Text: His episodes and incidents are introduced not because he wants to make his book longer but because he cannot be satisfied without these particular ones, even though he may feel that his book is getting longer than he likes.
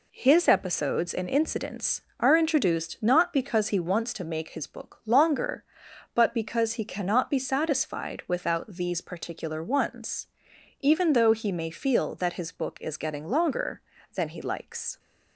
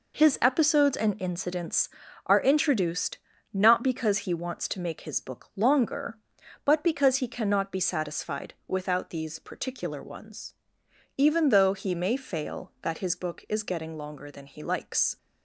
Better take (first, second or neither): first